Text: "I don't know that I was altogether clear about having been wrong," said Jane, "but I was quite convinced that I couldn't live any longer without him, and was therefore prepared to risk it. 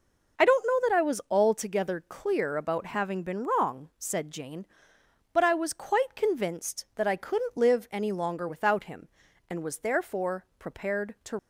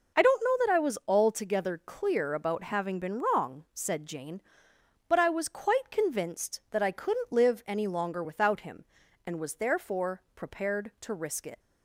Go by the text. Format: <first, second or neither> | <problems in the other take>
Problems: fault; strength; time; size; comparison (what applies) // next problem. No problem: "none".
second | stops before "risk it"; at 11.3 s